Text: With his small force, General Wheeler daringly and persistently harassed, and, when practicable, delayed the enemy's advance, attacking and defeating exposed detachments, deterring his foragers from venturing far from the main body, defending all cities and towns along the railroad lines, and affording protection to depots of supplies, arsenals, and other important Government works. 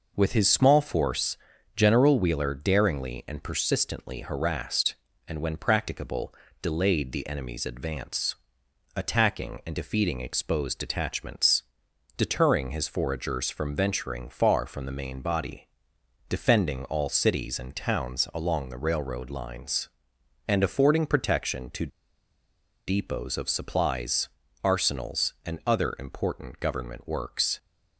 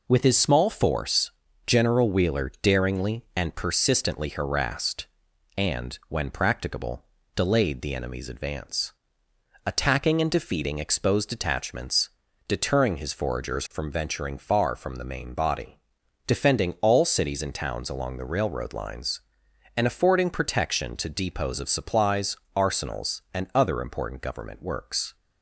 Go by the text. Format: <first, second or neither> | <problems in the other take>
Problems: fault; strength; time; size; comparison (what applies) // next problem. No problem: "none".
second | pauses between "to" and "depots"; at 21.8 s; 0.99 s long